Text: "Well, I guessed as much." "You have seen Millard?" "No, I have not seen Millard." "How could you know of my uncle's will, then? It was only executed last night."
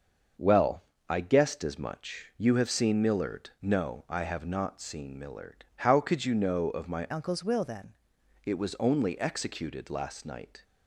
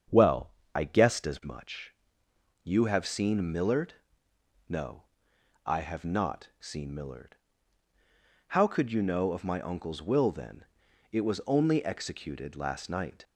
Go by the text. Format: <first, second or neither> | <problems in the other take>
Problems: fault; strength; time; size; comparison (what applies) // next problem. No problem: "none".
second | starts louder than the rest; until 1.6 s; 6.5 dB; strong in the second // changes voice from "uncle's" to "then"; from 7.1 to 7.9 s; 0.8 s long